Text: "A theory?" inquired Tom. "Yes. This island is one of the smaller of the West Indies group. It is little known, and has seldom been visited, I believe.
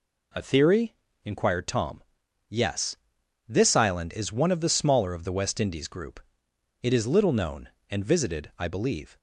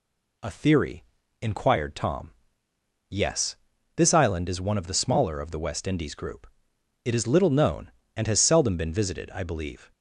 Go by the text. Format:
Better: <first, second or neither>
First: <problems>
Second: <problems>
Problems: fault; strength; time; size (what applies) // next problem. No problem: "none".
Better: second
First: skips "has seldom been"; at 8.0 s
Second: none